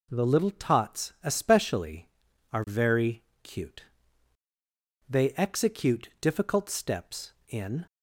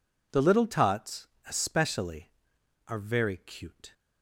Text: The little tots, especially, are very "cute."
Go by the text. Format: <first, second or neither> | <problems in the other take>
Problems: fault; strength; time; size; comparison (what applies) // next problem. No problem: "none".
second | pauses between "very" and "cute"; slight; at 3.2 s; 0.22 s long // goes on to say "They execute difficult steps in"; strong; from 5.0 s on; 2.7 s long